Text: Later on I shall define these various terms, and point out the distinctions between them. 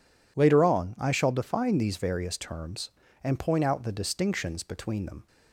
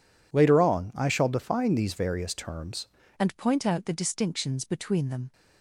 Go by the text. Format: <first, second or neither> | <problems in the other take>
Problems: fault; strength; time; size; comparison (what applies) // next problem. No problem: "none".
first | changes voice at "and"; from 3.1 s on; 2.2 s long